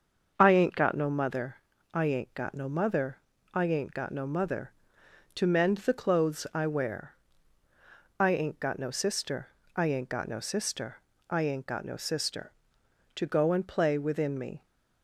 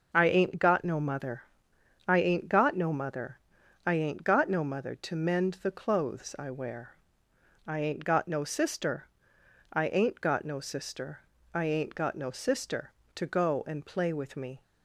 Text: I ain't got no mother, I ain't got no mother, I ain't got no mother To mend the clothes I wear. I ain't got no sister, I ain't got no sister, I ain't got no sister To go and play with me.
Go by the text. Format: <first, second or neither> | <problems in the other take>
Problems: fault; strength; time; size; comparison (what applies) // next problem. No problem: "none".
second | starts louder than the rest; until 1.3 s; 6.5 dB // says "within" for "with"; at 13.9 s